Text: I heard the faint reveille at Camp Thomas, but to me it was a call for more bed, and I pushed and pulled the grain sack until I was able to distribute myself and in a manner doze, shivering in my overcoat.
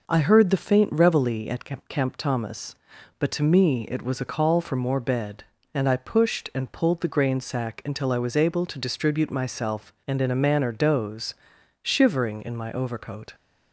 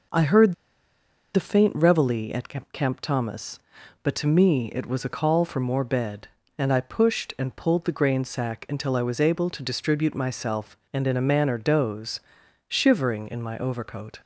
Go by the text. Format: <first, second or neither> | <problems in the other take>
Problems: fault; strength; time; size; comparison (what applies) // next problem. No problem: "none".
first | pauses between "heard" and "the"; noticeable; at 0.5 s; 0.80 s long